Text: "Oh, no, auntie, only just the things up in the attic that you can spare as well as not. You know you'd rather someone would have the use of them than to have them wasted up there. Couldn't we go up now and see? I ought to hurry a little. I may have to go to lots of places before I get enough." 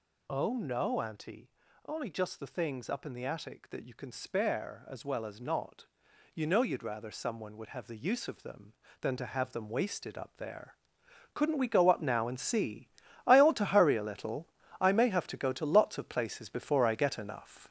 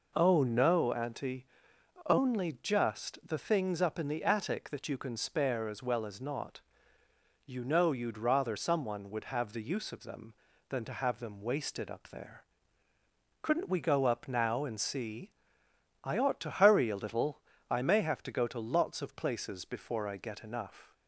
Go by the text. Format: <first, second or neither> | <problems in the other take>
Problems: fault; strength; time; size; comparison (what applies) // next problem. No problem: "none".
second | gets louder; noticeable; throughout; 5.5 dB